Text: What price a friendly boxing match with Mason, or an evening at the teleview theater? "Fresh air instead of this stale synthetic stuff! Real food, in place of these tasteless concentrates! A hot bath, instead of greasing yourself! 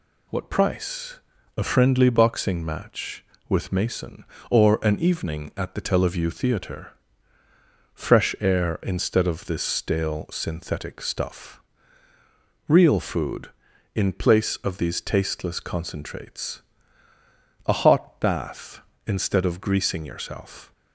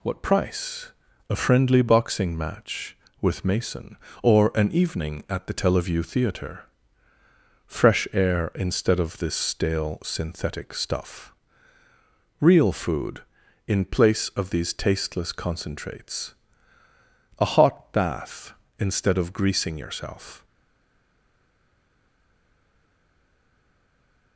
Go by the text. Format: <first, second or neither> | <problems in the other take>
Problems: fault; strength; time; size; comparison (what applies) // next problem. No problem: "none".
first | pauses between "price" and "a"; slight; at 0.9 s; 0.36 s long; slight in the first // stays silent after the last word; strong; from 20.4 s on; 3.9 s long